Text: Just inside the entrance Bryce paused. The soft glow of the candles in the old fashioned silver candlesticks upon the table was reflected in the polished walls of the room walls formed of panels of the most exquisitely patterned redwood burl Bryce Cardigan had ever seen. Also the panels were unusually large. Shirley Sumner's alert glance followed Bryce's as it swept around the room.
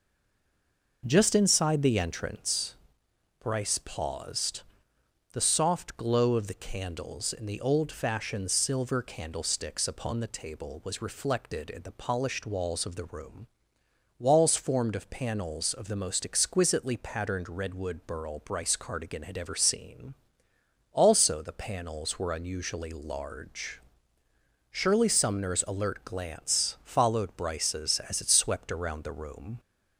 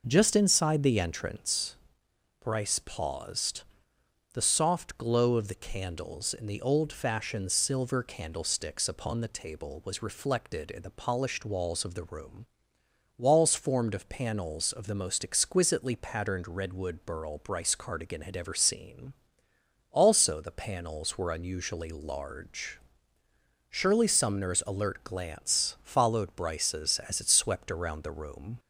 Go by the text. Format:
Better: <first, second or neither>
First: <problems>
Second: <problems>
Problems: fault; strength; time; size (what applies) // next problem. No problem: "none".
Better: second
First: stays silent before the first word; until 1.0 s; 1.0 s long // pauses between "entrance" and "Bryce"; noticeable; at 2.7 s; 0.62 s long // pauses between "room" and "walls"; noticeable; at 13.4 s; 0.72 s long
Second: pauses between "entrance" and "Bryce"; noticeable; at 1.7 s; 0.62 s long // pauses between "room" and "walls"; noticeable; at 12.4 s; 0.72 s long